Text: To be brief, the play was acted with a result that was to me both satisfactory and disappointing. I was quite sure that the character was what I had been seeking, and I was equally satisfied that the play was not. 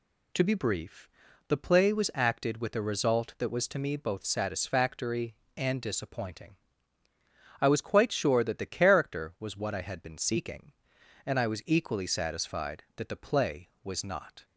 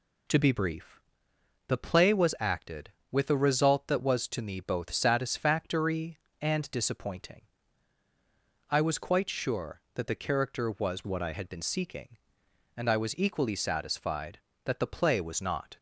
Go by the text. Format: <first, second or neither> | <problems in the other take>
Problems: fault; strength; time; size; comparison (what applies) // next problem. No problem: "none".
first | changes voice from "what" to "I"; from 11.0 to 11.3 s; 0.3 s long